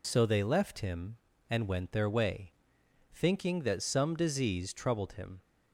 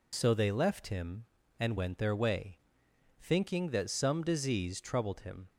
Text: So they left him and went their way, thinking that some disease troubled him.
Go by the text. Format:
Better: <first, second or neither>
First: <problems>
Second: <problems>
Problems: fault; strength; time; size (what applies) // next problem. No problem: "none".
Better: neither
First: none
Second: none